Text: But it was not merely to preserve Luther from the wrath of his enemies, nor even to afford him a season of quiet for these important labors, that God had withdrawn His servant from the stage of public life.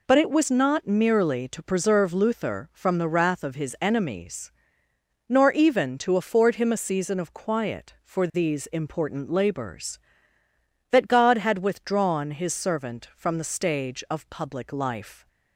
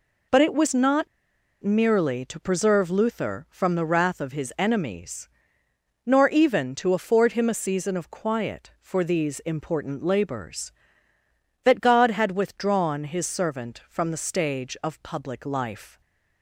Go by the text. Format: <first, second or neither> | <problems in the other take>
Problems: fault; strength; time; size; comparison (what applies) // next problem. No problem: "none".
first | pauses between "not" and "merely"; noticeable; at 1.0 s; 0.56 s long // stays silent after the last word; slight; from 15.9 s on; 0.5 s long